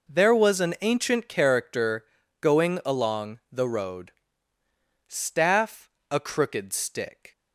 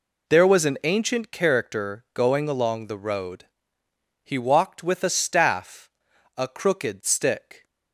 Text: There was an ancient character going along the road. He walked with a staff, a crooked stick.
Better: second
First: pauses between "character" and "going"; slight; at 2.0 s; 0.36 s long // skips "He walked with a"; at 4.6 s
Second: none

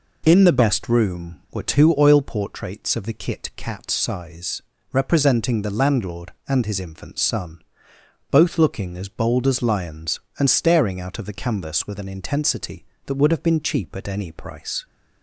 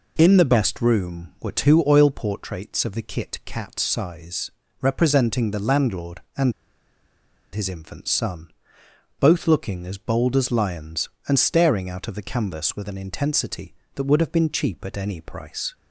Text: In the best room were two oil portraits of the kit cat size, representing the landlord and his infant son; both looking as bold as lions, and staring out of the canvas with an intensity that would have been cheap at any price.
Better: first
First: none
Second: pauses between "and" and "his"; at 6.5 s; 1.0 s long

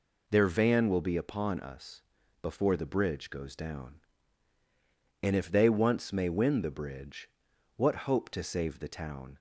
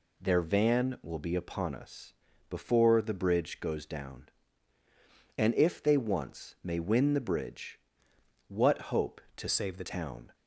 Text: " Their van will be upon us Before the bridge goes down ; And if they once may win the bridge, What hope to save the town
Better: first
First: pauses between "us" and "Before"; at 2.0 s; 0.40 s long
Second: pauses between "us" and "Before"; slight; at 2.1 s; 0.36 s long // changes voice from "save" to "the"; from 9.4 to 9.8 s; 0.4 s long

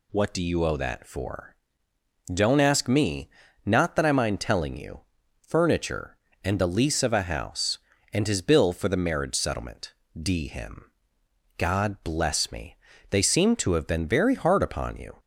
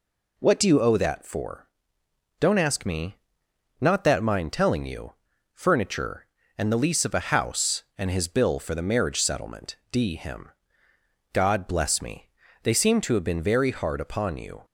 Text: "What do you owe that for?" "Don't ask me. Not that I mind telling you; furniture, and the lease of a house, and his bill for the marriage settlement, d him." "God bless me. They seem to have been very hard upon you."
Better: first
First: none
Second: skips "I"; at 4.2 s

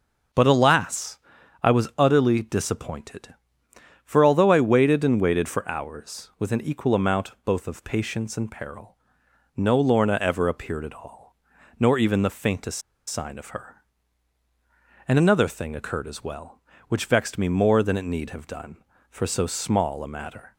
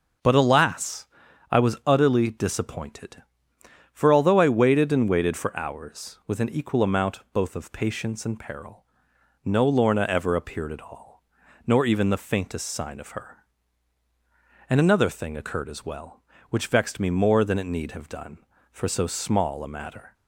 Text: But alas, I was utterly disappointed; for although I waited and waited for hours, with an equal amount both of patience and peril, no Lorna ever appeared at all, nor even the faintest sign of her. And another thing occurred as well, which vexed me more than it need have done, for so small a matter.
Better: second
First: starts louder than the rest; until 1.7 s; 6.5 dB // pauses between "faintest" and "sign"; slight; at 12.7 s; 0.27 s long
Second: starts louder than the rest; until 1.6 s; 6.5 dB

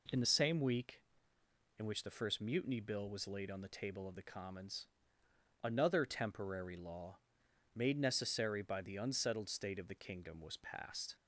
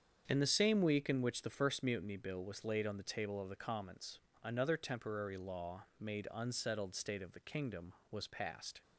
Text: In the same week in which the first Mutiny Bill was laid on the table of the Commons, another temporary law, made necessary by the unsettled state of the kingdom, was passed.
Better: first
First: none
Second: starts louder than the rest; strong; until 1.2 s; 7.5 dB // skips "necessary by the"; at 6.3 s

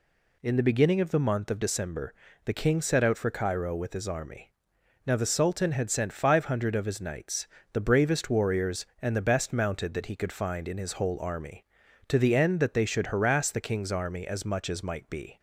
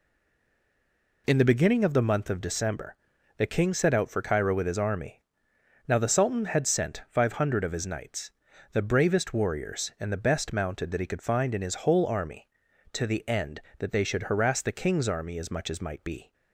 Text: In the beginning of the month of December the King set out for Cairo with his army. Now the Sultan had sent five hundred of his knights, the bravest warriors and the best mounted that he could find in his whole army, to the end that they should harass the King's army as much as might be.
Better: first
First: pauses between "December" and "the"; slight; at 2.1 s; 0.30 s long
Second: stays silent before the first word; noticeable; until 1.2 s; 1.2 s long // pauses between "December" and "the"; at 2.9 s; 0.42 s long

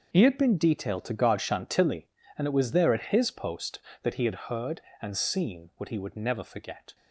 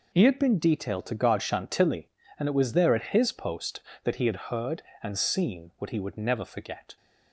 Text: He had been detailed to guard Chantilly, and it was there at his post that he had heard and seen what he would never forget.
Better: second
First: gets quieter; strong; throughout; 12 dB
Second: none

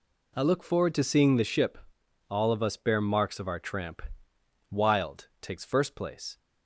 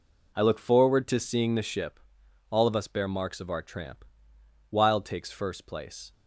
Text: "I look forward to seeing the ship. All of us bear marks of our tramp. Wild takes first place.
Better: neither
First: none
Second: none

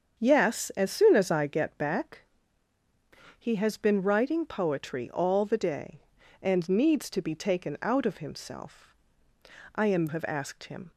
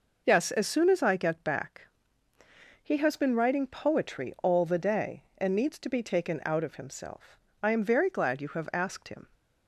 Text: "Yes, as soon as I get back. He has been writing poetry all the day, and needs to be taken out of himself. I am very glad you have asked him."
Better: second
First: starts louder than the rest; strong; until 1.2 s; 7 dB // skips "very glad you"; at 10.0 s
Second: none

